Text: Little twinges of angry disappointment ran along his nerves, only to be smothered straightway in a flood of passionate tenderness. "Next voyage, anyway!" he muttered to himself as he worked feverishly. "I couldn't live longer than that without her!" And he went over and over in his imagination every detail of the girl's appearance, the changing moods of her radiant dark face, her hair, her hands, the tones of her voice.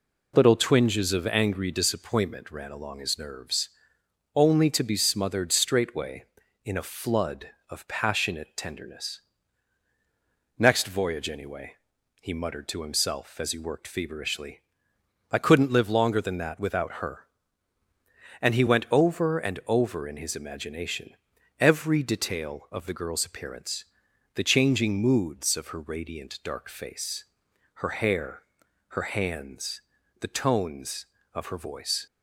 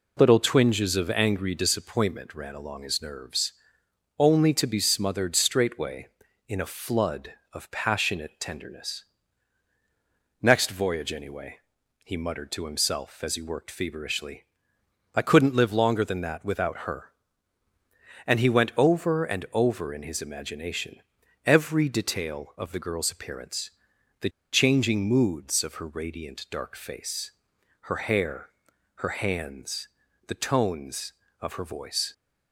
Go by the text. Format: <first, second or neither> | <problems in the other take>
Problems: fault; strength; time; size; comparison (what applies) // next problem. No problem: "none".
first | pauses between "imagination" and "every"; noticeable; at 20.9 s; 0.46 s long; noticeable in the first // pauses between "the" and "changing"; slight; at 24.2 s; 0.22 s long